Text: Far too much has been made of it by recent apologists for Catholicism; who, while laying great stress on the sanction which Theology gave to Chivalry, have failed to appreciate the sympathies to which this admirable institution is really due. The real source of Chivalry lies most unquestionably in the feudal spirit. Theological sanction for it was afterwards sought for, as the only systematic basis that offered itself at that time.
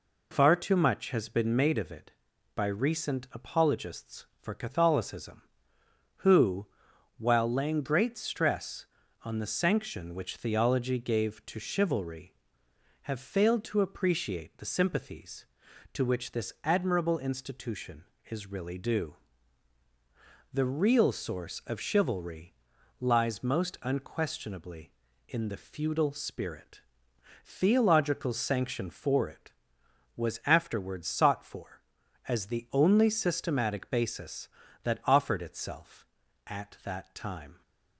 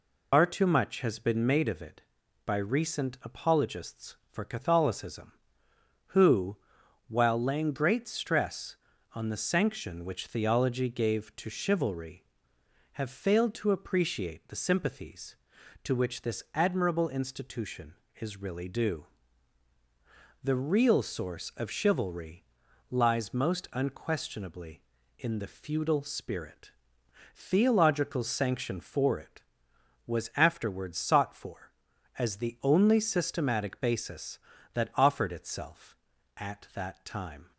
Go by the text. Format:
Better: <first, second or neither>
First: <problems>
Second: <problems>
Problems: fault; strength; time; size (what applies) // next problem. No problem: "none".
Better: first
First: pauses between "Chivalry" and "lies"; noticeable; at 22.5 s; 0.48 s long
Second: loses the start of "Far"; at 0.3 s; 115 ms // pauses between "Chivalry" and "lies"; noticeable; at 22.4 s; 0.48 s long